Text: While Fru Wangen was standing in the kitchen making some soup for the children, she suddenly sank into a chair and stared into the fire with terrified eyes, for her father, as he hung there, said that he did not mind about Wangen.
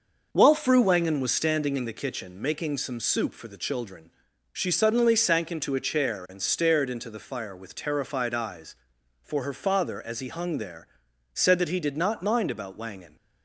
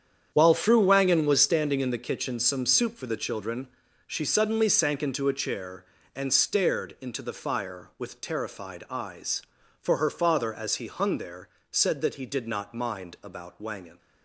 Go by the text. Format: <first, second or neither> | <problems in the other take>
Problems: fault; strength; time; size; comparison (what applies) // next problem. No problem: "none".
first | starts louder than the rest; strong; until 1.3 s; 8.5 dB // skips "making"; at 2.3 s